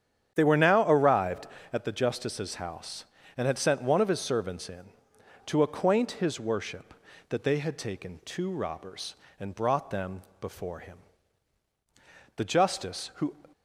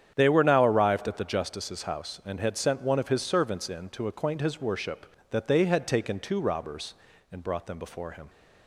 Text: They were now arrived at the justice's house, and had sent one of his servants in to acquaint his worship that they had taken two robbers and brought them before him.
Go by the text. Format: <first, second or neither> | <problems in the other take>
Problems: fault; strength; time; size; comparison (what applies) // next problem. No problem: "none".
second | starts louder than the rest; strong; until 1.3 s; 9 dB; strong in the second // pauses between "them" and "before"; slight; at 10.2 s; 0.18 s long // goes on to say "The justice who"; noticeable; from 12.3 s on; 1.0 s long